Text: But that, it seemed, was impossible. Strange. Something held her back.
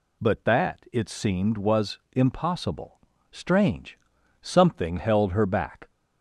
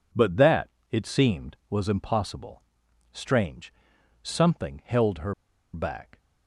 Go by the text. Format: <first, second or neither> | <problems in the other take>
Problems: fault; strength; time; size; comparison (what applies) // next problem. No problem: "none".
first | pauses between "her" and "back"; at 5.3 s; 0.39 s long